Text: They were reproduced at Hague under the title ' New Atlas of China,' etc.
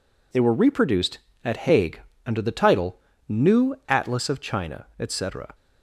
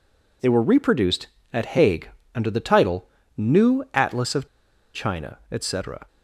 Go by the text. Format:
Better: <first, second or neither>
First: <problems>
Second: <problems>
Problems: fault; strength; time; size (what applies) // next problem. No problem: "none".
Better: first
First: pauses between "Hague" and "under"; slight; at 1.9 s; 0.26 s long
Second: pauses between "Hague" and "under"; slight; at 2.0 s; 0.26 s long // pauses between "of" and "China"; noticeable; at 4.4 s; 0.47 s long